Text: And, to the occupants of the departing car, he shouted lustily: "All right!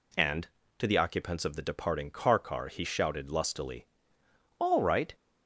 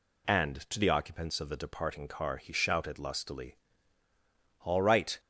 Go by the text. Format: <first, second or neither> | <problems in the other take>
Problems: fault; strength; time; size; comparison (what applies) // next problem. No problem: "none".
second | says "car" twice; at 2.3 s